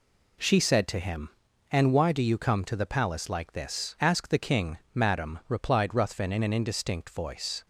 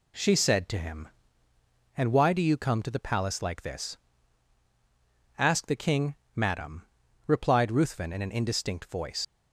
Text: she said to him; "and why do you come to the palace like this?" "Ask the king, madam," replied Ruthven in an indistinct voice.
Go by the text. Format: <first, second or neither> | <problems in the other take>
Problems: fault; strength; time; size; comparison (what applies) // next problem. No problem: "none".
first | leaves "voice" unfinished; at 9.2 s; 80 ms